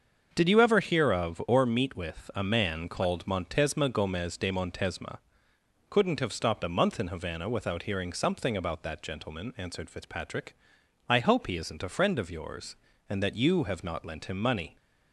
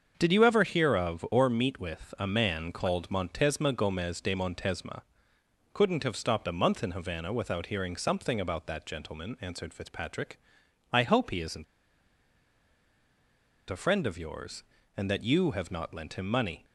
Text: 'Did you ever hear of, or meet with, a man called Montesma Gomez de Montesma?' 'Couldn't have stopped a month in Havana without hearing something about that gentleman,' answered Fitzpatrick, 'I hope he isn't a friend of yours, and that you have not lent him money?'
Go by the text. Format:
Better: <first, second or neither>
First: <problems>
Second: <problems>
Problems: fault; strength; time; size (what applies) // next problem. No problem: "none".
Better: first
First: starts louder than the rest; until 1.3 s; 6.5 dB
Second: starts louder than the rest; until 1.1 s; 6.5 dB // pauses between "isn't" and "a"; strong; at 11.6 s; 2.0 s long